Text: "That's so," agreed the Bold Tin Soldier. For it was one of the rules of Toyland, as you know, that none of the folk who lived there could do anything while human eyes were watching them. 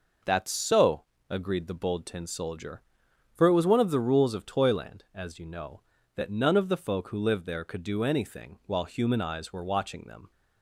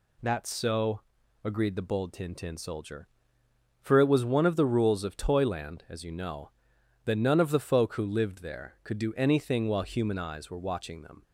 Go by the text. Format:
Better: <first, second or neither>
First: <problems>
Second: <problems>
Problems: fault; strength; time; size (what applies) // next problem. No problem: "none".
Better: first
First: none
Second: says "Tin" twice; at 2.3 s